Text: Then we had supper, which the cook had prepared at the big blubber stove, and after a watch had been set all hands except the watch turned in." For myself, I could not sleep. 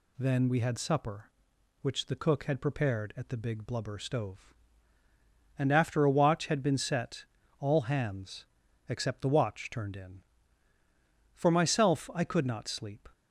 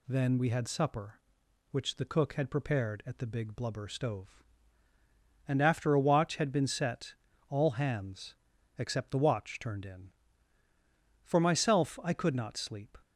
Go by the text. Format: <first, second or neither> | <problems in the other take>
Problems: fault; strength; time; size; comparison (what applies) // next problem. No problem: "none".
neither | pauses between "set" and "all"; slight; the same in both // pauses between "hands" and "except"; the same in both